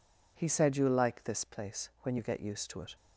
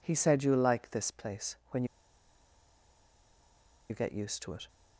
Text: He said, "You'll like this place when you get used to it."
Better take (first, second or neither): first